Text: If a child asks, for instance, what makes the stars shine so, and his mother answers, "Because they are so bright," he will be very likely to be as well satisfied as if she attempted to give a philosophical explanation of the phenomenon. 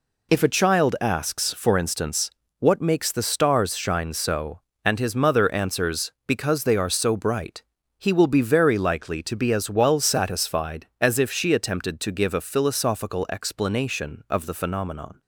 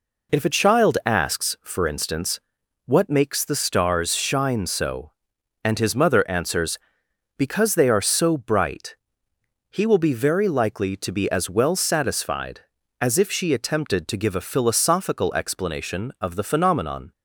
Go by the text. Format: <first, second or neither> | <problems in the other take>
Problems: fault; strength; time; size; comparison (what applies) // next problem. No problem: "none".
neither | none